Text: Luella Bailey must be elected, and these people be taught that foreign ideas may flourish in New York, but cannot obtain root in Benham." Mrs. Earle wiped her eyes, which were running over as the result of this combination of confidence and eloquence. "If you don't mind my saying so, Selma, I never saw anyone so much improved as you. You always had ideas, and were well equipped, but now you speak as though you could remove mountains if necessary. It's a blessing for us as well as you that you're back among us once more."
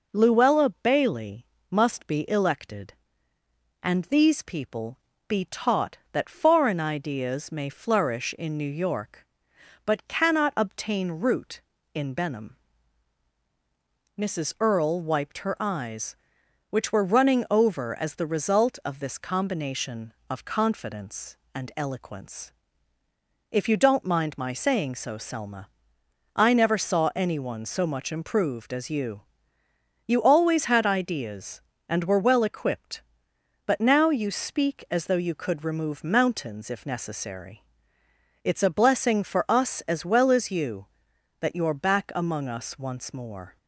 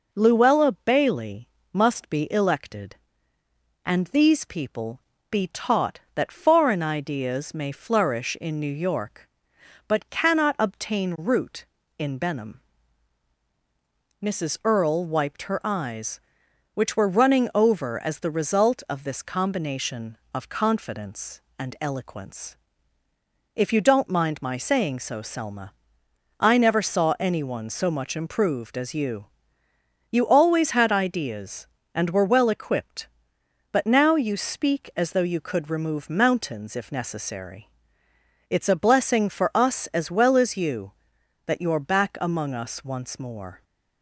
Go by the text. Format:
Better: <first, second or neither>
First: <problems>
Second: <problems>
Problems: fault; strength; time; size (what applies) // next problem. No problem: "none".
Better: neither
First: pauses between "Bailey" and "must"; slight; at 1.4 s; 0.24 s long // pauses between "people" and "be"; slight; at 4.9 s; 0.30 s long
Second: pauses between "Bailey" and "must"; slight; at 1.4 s; 0.24 s long // pauses between "people" and "be"; slight; at 4.9 s; 0.30 s long